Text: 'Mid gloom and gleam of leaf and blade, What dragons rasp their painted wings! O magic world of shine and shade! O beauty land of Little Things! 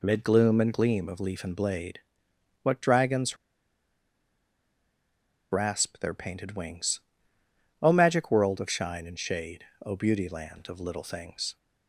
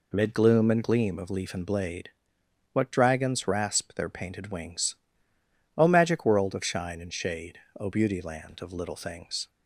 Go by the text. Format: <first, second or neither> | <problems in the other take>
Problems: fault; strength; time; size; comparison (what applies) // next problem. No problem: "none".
second | pauses between "dragons" and "rasp"; strong; at 3.3 s; 2.1 s long